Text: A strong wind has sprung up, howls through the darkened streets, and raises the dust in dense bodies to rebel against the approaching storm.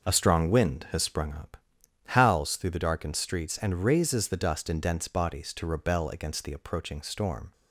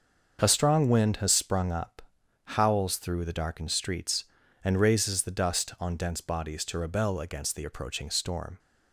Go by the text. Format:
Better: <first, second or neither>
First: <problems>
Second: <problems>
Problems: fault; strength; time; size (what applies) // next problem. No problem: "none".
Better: first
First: none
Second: starts louder than the rest; until 1.4 s; 6.5 dB // says "on" for "in"; at 5.7 s